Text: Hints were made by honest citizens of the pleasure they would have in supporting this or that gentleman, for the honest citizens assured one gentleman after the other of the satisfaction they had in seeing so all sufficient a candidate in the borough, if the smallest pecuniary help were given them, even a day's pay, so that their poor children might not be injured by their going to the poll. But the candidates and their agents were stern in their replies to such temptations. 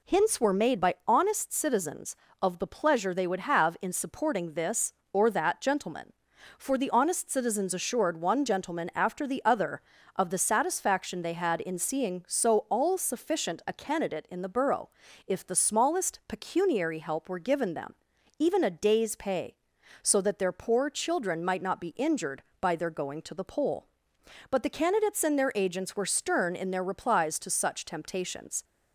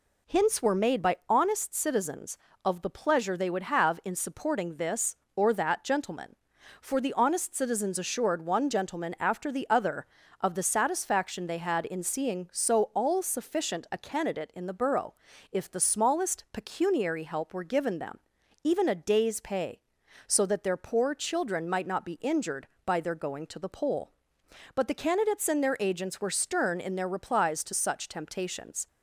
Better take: neither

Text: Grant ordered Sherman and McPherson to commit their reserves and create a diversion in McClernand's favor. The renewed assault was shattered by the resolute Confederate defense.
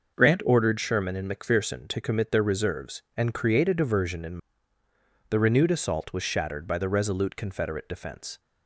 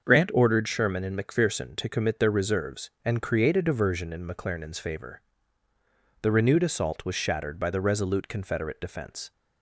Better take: second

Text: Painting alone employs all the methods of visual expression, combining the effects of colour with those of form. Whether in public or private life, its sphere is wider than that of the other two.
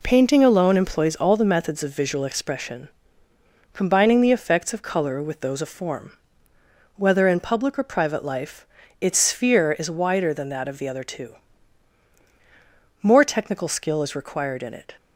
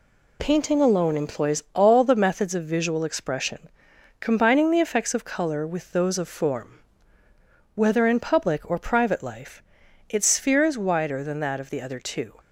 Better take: second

